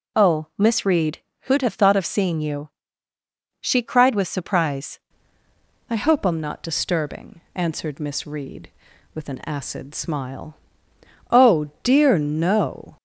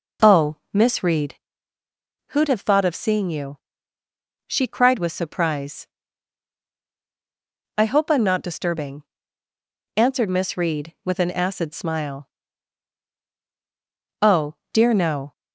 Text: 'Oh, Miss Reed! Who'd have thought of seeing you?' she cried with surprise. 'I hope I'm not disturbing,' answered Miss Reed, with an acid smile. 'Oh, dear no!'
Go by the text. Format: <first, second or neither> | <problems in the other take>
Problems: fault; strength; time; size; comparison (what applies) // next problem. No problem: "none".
second | changes voice at "I"; from 5.9 s on; 7.0 s long